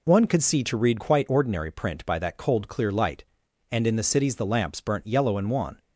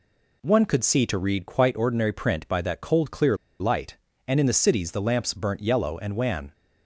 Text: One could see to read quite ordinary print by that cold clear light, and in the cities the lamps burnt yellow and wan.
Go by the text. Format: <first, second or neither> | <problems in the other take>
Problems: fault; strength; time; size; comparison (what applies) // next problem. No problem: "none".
first | pauses between "clear" and "light"; slight; at 3.3 s; 0.24 s long